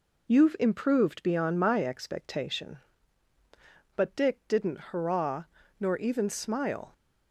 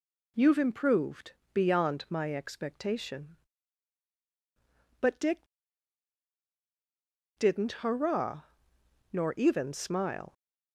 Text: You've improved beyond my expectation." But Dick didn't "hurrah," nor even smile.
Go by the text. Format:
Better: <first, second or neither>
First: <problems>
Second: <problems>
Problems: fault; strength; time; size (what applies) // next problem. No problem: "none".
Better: first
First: none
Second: pauses between "improved" and "beyond"; slight; at 1.3 s; 0.22 s long // pauses between "Dick" and "didn't"; strong; at 5.4 s; 1.9 s long